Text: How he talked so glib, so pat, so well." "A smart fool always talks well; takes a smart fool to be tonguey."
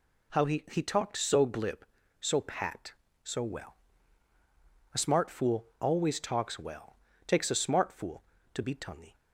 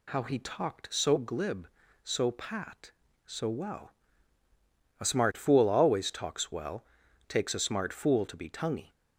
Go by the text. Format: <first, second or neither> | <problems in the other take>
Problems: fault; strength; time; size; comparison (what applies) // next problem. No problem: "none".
second | says "he" twice; at 0.7 s